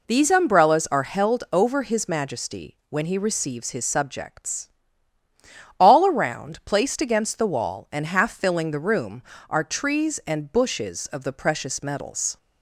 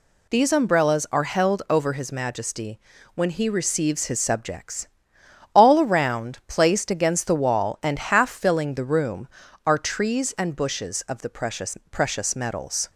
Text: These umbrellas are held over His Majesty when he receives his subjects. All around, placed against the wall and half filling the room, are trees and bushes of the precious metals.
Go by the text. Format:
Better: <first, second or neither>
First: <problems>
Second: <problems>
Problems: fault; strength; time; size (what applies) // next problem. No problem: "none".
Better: first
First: none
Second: pauses between "Majesty" and "when"; slight; at 2.7 s; 0.34 s long // says "precious" twice; at 11.9 s